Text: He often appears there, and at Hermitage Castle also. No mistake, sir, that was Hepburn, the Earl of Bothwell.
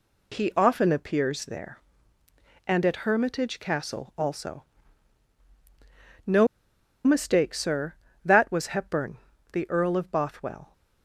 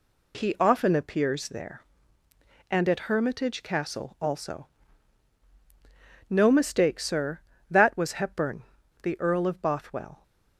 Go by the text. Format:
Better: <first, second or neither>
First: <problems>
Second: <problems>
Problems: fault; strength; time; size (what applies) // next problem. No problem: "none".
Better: second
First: pauses between "No" and "mistake"; noticeable; at 6.4 s; 0.59 s long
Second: none